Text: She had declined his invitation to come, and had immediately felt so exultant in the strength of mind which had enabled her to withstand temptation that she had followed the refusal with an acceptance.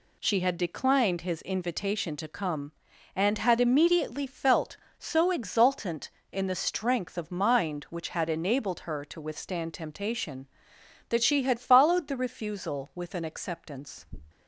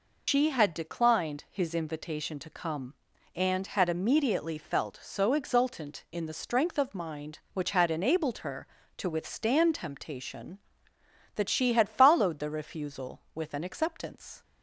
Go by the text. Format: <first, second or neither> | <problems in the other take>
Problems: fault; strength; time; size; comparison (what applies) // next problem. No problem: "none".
first | loses the start of "She"; at 0.2 s; 115 ms